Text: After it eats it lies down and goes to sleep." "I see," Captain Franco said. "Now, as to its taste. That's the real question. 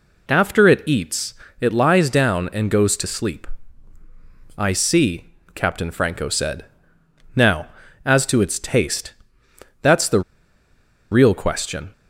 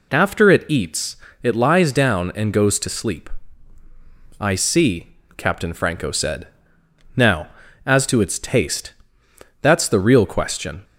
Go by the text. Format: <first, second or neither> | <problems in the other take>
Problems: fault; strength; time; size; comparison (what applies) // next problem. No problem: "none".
second | pauses between "eats" and "it"; slight; at 1.3 s; 0.26 s long; slight in the second // pauses between "the" and "real"; noticeable; at 10.2 s; 0.91 s long